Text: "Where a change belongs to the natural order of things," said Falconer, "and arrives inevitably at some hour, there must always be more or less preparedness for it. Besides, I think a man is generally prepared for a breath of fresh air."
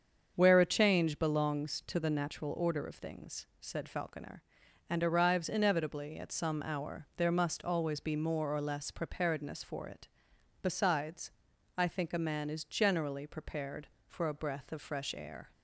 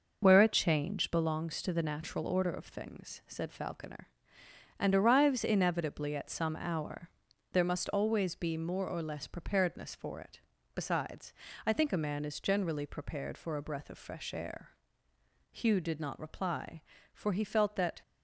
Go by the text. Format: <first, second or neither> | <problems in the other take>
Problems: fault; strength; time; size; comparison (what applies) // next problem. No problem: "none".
first | starts louder than the rest; noticeable; until 1.2 s; 6 dB; strong in the first // goes on to say "Hugh did not reply for he felt that"; strong; from 15.5 s on; 2.4 s long